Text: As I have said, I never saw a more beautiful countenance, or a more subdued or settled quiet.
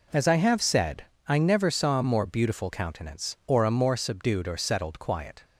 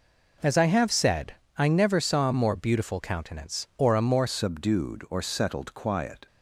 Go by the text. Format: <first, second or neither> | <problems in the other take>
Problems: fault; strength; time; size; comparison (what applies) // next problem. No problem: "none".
first | changes voice at "subdued"; from 4.2 s on; 2.0 s long